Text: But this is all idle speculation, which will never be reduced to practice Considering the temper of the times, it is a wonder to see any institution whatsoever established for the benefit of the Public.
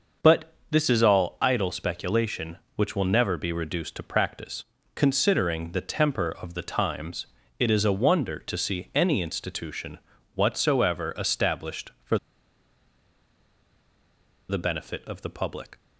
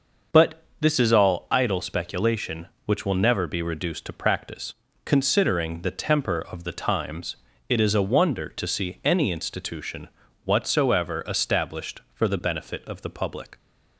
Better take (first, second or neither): second